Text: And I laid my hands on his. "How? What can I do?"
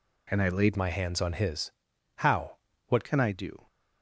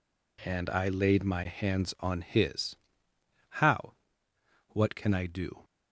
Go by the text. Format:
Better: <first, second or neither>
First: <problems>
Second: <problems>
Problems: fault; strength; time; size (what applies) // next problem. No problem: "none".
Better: second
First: changes voice from "my" to "What"; from 0.7 to 3.0 s; 2.3 s long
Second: none